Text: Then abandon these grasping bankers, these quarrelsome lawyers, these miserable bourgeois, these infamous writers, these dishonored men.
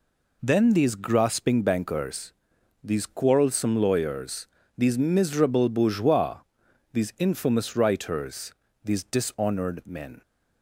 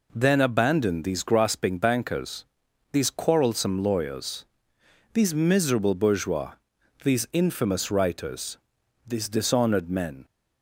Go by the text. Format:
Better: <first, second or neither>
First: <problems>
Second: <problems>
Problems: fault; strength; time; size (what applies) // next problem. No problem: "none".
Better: second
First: skips "abandon"; at 0.7 s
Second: none